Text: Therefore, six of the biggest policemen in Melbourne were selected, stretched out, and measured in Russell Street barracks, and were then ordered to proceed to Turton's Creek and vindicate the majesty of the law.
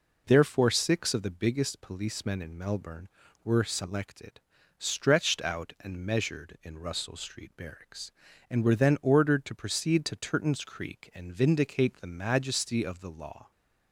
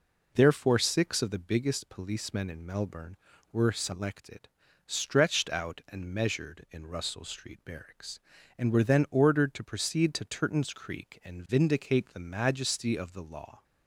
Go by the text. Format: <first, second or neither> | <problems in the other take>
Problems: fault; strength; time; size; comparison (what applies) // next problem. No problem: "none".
neither | none